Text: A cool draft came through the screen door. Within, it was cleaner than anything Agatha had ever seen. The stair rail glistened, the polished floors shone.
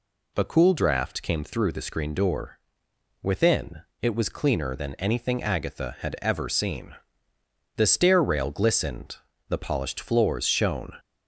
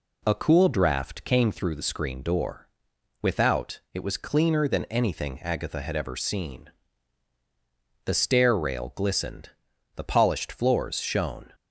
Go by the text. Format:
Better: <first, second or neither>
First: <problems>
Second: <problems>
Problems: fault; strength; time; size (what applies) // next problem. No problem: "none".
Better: first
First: none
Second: says "Without" for "Within"; at 3.2 s